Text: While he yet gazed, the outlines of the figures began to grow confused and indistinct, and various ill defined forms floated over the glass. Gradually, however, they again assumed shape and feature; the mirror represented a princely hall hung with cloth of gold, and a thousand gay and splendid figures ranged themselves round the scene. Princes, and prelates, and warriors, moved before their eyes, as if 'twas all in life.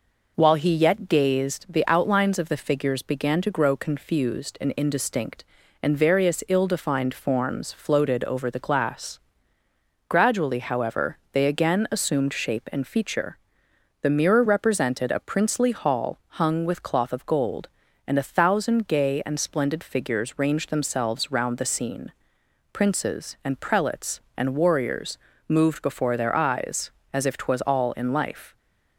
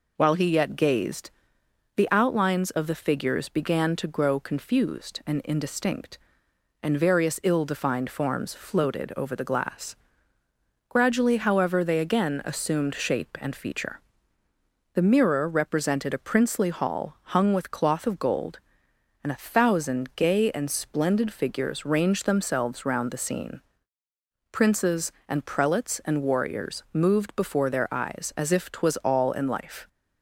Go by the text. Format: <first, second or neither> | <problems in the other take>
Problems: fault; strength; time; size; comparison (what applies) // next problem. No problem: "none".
neither | none